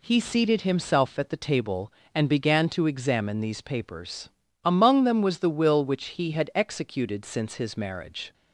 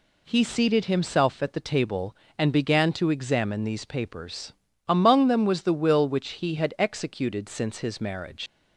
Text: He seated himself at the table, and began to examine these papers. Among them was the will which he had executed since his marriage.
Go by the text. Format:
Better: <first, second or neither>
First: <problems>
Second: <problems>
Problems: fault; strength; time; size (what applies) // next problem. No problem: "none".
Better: first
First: none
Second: leaves "marriage" unfinished; at 8.4 s; 105 ms